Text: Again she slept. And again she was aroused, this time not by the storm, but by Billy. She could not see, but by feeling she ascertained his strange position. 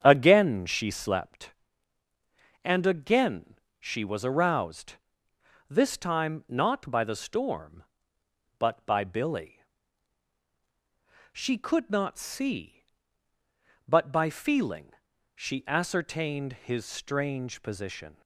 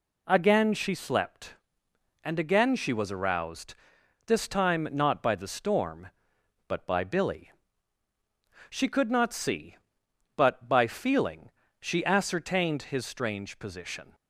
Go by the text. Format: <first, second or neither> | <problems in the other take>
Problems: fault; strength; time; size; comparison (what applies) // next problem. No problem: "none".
second | starts louder than the rest; strong; until 1.3 s; 8.5 dB // pauses between "again" and "she"; slight; at 3.5 s; 0.24 s long // pauses between "feeling" and "she"; noticeable; at 14.8 s; 0.46 s long; slight in the second